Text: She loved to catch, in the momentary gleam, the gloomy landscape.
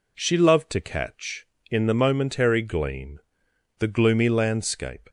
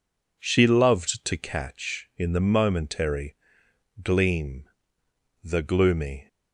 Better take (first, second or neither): first